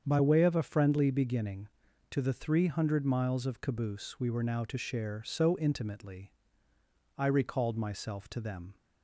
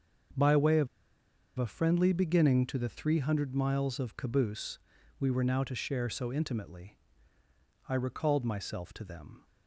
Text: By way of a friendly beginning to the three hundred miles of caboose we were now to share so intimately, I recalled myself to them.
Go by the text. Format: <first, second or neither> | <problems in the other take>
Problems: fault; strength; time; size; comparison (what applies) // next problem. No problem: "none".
first | starts louder than the rest; until 2.0 s; 6.5 dB; strong in the first // pauses between "of" and "a"; noticeable; at 0.8 s; 0.70 s long // pauses between "caboose" and "we"; at 4.7 s; 0.42 s long